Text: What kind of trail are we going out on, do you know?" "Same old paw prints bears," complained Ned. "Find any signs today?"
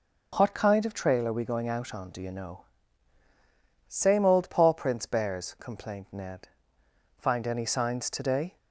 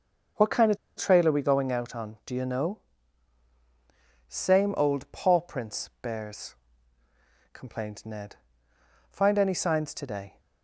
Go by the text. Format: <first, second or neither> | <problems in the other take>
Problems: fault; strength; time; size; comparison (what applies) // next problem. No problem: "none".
first | starts louder than the rest; noticeable; until 1.5 s; 6 dB // pauses between "of" and "trail"; slight; at 0.7 s; 0.19 s long